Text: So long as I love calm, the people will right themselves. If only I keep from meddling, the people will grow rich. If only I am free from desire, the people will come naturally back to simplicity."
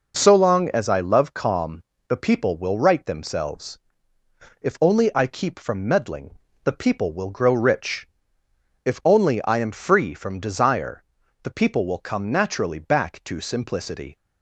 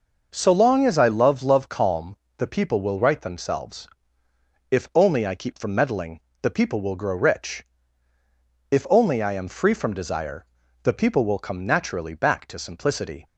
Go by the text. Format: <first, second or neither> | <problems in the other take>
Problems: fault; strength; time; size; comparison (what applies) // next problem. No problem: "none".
first | says "love" twice; at 1.4 s